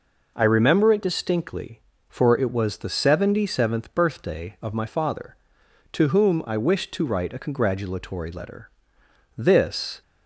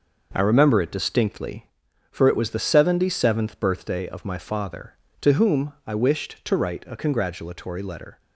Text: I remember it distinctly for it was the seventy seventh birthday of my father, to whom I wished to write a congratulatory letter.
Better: second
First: goes on to say "This"; noticeable; from 9.3 s on; 0.64 s long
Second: none

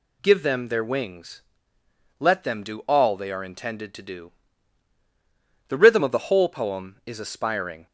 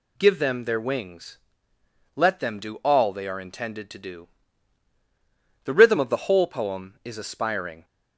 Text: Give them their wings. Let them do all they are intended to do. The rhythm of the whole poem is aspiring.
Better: neither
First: none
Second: none

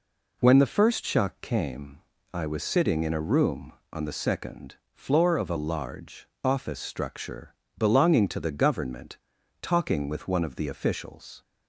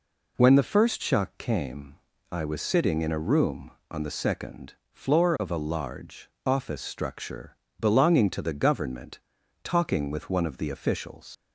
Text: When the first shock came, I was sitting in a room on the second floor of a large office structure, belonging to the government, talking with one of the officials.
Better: first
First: pauses between "second" and "floor"; slight; at 4.7 s; 0.18 s long // pauses between "large" and "office"; slight; at 6.2 s; 0.16 s long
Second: pauses between "second" and "floor"; slight; at 4.7 s; 0.18 s long // pauses between "large" and "office"; slight; at 6.2 s; 0.16 s long // leaves "officials" unfinished; at 11.3 s; 85 ms

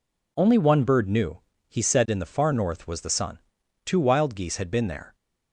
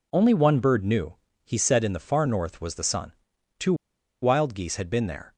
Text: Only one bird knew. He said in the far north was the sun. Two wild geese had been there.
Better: first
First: none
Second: pauses between "Two" and "wild"; noticeable; at 3.7 s; 0.48 s long

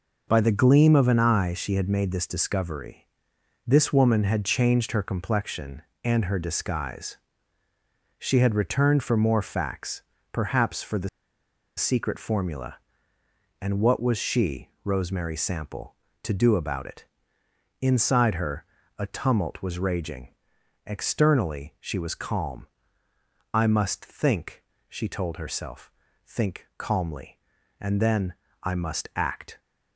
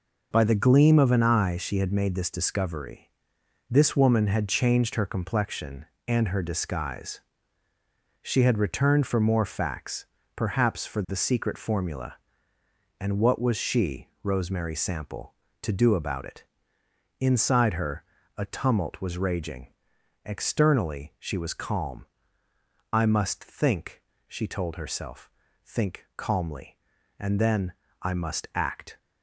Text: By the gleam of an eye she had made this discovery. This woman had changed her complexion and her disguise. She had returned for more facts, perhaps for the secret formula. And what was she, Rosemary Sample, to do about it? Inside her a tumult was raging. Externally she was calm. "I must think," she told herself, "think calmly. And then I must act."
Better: second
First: pauses between "the" and "secret"; noticeable; at 11.0 s; 0.68 s long // pauses between "her" and "a"; slight; at 18.6 s; 0.32 s long // pauses between "then" and "I"; slight; at 28.3 s; 0.30 s long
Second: pauses between "her" and "a"; slight; at 18.0 s; 0.32 s long // pauses between "then" and "I"; slight; at 27.7 s; 0.30 s long

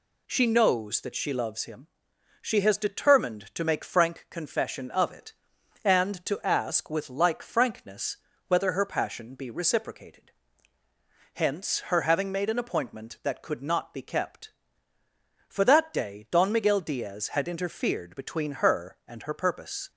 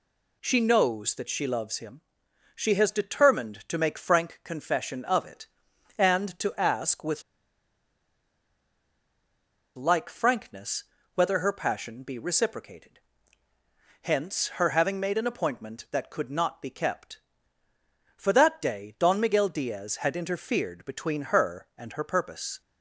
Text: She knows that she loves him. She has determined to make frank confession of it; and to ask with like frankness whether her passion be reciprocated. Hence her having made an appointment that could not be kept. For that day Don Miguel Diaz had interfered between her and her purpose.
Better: first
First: pauses between "frankness" and "whether"; slight; at 8.1 s; 0.30 s long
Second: pauses between "with" and "like"; strong; at 7.2 s; 2.5 s long // pauses between "frankness" and "whether"; slight; at 10.8 s; 0.30 s long

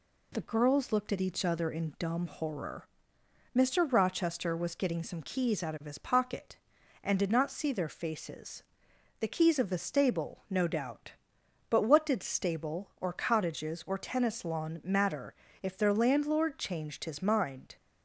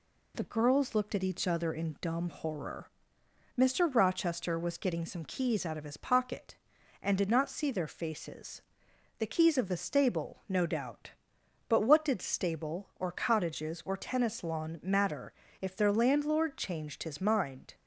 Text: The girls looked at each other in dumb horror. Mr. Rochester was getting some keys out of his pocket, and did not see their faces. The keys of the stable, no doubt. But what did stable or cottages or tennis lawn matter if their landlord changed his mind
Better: neither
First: pauses between "matter" and "if"; slight; at 15.3 s; 0.28 s long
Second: pauses between "matter" and "if"; slight; at 15.3 s; 0.28 s long

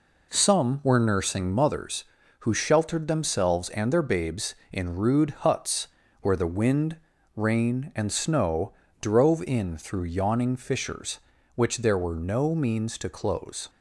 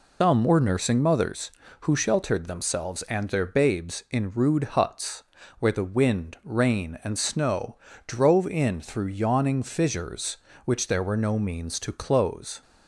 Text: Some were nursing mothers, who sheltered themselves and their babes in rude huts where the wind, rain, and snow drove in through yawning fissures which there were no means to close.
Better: first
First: pauses between "huts" and "where"; slight; at 5.8 s; 0.34 s long // pauses between "snow" and "drove"; slight; at 8.7 s; 0.30 s long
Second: loses the start of "Some"; at 0.2 s; 130 ms // pauses between "huts" and "where"; slight; at 5.2 s; 0.34 s long // pauses between "snow" and "drove"; slight; at 7.7 s; 0.30 s long

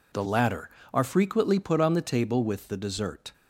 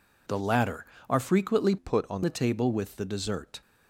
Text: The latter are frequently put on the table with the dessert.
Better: first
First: none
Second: changes voice from "put" to "on"; from 1.7 to 2.2 s; 0.5 s long

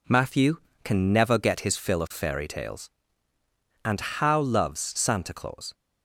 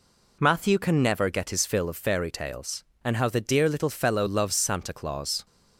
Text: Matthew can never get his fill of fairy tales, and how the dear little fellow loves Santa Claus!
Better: second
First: skips "the dear little fellow"; at 4.3 s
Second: none

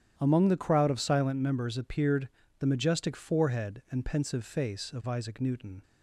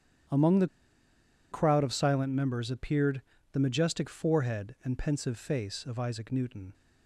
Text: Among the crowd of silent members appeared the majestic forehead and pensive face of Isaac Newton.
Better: first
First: starts louder than the rest; strong; until 1.1 s; 10 dB // pauses between "appeared" and "the"; slight; at 2.2 s; 0.30 s long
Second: starts louder than the rest; strong; until 2.1 s; 10.5 dB // pauses between "the" and "crowd"; noticeable; at 0.6 s; 0.84 s long // pauses between "appeared" and "the"; slight; at 3.2 s; 0.30 s long

